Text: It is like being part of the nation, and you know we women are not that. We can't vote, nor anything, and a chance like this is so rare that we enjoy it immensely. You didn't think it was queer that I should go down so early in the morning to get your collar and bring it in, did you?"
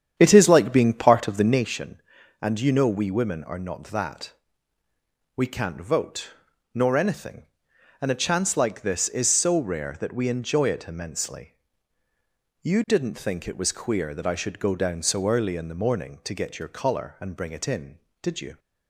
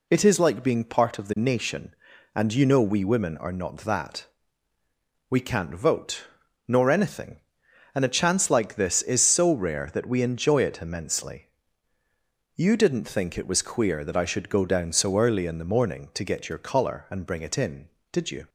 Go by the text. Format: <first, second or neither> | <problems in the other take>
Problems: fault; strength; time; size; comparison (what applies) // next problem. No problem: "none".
second | starts louder than the rest; strong; until 1.7 s; 9 dB